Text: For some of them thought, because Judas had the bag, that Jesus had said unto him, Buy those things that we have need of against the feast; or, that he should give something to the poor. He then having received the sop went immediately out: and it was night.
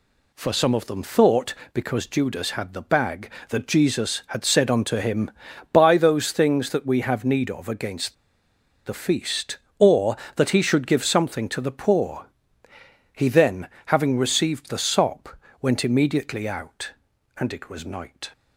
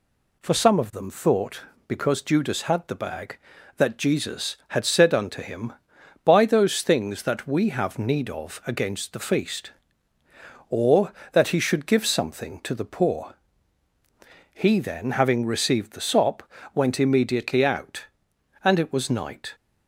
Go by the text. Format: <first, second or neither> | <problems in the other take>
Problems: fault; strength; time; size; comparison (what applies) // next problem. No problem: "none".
second | pauses between "against" and "the"; noticeable; at 8.1 s; 0.71 s long // pauses between "then" and "having"; slight; at 13.6 s; 0.18 s long // pauses between "sop" and "went"; slight; at 15.3 s; 0.24 s long; slight in the second